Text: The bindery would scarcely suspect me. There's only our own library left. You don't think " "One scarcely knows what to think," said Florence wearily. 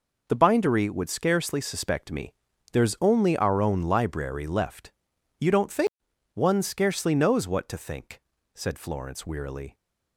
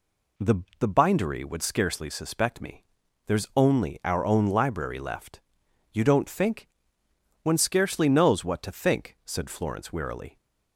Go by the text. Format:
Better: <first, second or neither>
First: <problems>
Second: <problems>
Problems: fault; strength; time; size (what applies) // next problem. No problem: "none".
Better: first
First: none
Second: says "The" twice; at 0.8 s